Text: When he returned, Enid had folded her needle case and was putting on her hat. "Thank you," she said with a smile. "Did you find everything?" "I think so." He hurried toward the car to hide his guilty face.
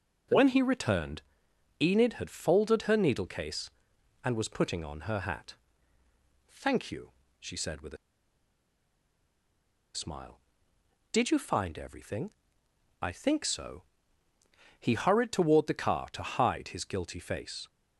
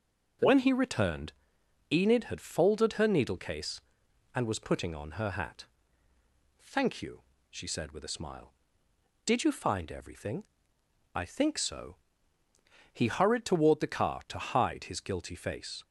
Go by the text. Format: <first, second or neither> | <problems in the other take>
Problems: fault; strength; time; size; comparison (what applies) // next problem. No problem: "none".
second | starts louder than the rest; noticeable; until 1.9 s; 6 dB; also in the second // pauses between "with" and "a"; strong; at 7.9 s; 1.9 s long